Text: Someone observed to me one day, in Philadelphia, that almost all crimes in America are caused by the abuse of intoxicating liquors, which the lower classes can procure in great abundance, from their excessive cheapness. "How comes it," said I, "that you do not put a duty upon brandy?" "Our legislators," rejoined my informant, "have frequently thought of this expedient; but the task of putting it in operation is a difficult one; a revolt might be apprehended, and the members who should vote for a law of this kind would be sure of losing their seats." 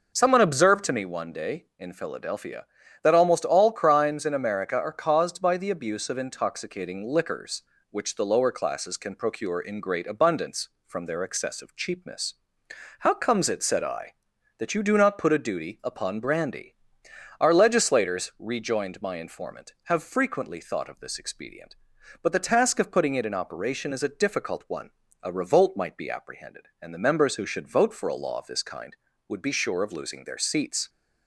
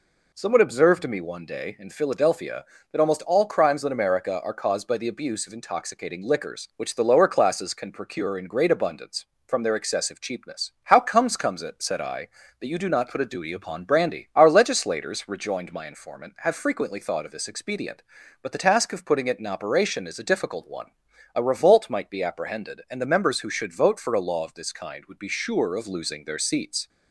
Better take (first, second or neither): first